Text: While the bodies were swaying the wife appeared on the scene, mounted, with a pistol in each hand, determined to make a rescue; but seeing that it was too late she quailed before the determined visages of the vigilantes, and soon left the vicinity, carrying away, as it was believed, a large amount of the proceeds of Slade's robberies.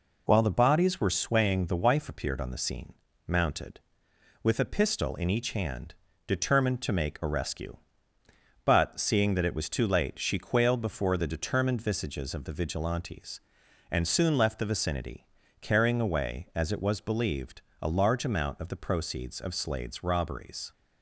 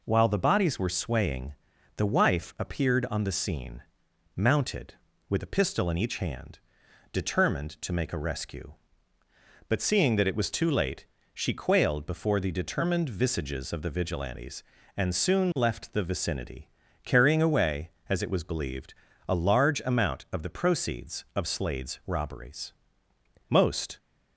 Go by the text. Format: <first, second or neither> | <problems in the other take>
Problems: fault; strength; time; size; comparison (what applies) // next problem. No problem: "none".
first | pauses between "swaying" and "the"; at 1.5 s; 0.44 s long // pauses between "late" and "she"; slight; at 11.0 s; 0.30 s long // goes on to say "Most"; slight; from 23.4 s on; 0.48 s long